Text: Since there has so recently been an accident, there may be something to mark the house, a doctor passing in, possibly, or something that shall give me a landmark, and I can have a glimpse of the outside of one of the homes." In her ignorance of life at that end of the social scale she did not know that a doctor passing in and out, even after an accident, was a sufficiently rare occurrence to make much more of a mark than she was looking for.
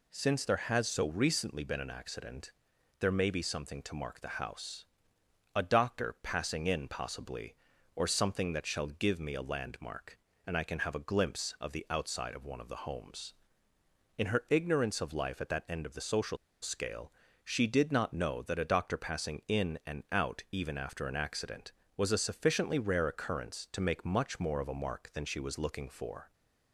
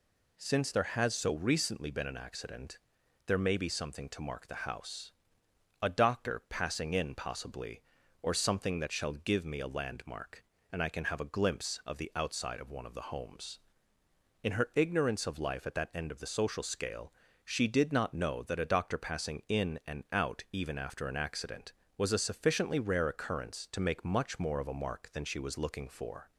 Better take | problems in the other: second | pauses between "social" and "scale"; slight; at 16.3 s; 0.27 s long // pauses between "scale" and "she"; slight; at 17.1 s; 0.32 s long; slight in the second

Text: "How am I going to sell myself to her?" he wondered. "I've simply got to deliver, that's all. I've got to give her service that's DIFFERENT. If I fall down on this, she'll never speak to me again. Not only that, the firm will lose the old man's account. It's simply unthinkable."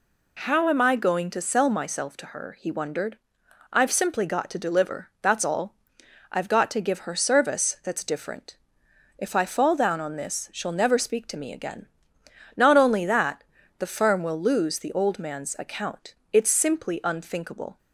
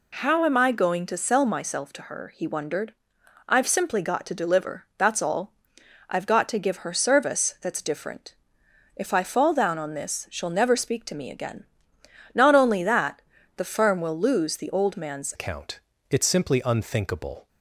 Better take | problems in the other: first | changes voice at "account"; from 15.3 s on; 2.1 s long

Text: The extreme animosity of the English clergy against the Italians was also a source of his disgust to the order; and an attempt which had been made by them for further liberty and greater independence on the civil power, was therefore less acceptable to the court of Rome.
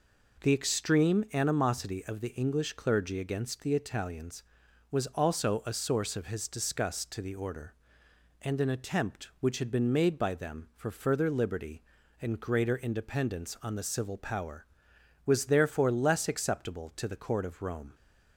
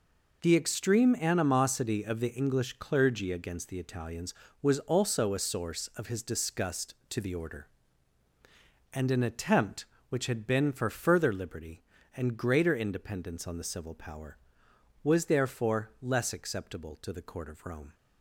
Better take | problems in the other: first | skips "made by them"; at 10.7 s

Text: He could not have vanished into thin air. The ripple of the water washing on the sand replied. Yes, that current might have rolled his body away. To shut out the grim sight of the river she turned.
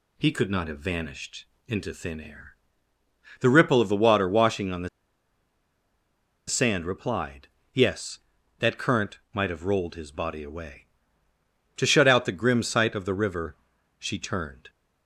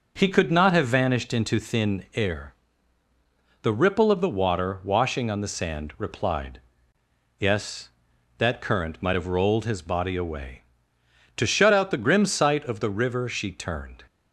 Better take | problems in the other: second | pauses between "vanished" and "into"; slight; at 1.4 s; 0.22 s long // pauses between "the" and "sand"; strong; at 4.8 s; 1.5 s long // pauses between "river" and "she"; at 13.5 s; 0.44 s long

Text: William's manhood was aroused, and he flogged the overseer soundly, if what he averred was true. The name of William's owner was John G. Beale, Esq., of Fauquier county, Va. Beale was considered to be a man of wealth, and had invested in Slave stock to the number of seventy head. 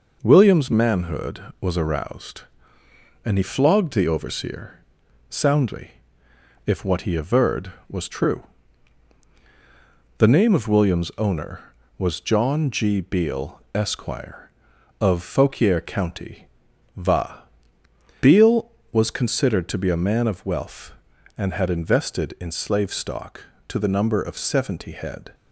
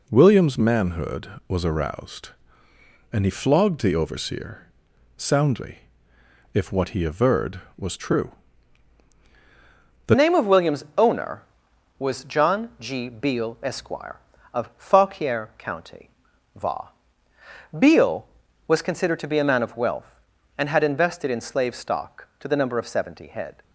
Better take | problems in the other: first | pauses between "overseer" and "soundly"; noticeable; at 4.6 s; 0.48 s long; noticeable in the first // changes voice at "name"; from 10.1 s on; 13.5 s long

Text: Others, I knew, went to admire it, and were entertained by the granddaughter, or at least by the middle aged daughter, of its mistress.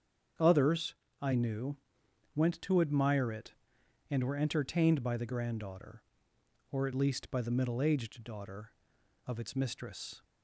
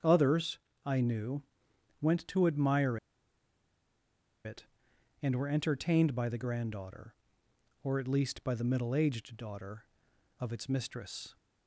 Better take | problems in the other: first | starts louder than the rest; strong; until 1.2 s; 7.5 dB; strong in the first // pauses between "admire" and "it"; strong; at 2.9 s; 1.4 s long

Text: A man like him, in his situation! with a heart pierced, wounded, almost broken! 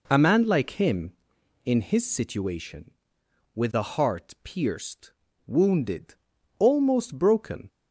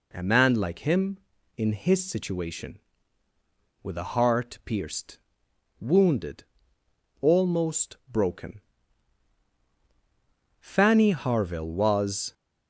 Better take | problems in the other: first | pauses between "almost" and "broken"; slight; at 7.9 s; 0.16 s long // goes on to say "Fanny Harville was"; strong; from 10.6 s on; 1.7 s long

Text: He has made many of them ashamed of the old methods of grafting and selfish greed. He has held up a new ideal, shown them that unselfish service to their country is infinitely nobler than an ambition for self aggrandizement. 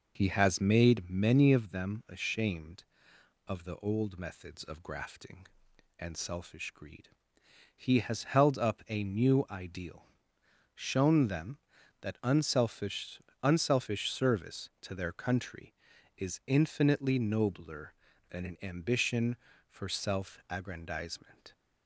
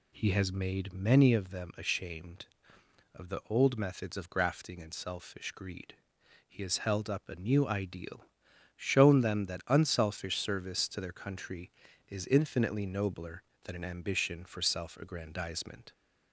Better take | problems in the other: second | says "unselfish" twice; at 13.4 s

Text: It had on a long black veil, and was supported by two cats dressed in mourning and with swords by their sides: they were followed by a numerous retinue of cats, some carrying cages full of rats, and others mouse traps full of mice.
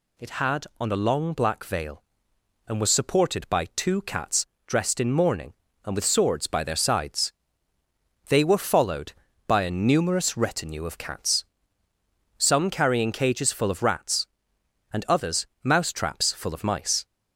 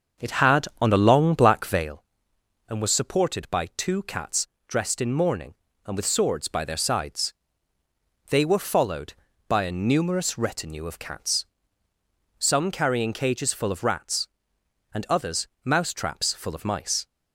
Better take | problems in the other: first | starts louder than the rest; until 1.9 s; 6.5 dB // pauses between "cats" and "dressed"; slight; at 4.4 s; 0.20 s long; slight in the first // pauses between "others" and "mouse"; slight; at 15.4 s; 0.18 s long; slight in the first

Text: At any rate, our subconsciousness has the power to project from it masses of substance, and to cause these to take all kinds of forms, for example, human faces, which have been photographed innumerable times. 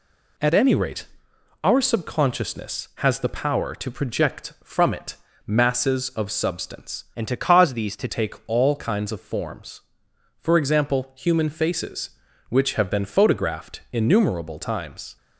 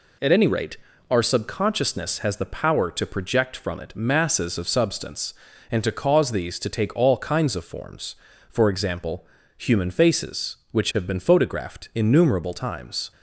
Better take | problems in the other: second | pauses between "it" and "masses"; slight; at 5.1 s; 0.30 s long // changes voice from "and" to "to"; from 7.1 to 8.0 s; 0.9 s long

